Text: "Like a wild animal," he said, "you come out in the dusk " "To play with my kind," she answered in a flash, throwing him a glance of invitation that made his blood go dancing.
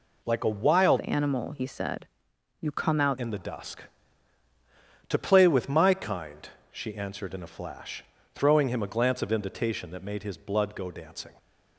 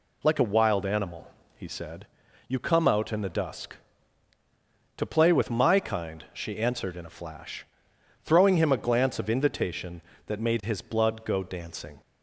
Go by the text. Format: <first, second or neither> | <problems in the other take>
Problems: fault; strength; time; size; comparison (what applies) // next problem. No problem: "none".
second | changes voice from "animal" to "out"; from 1.0 to 3.1 s; 2.1 s long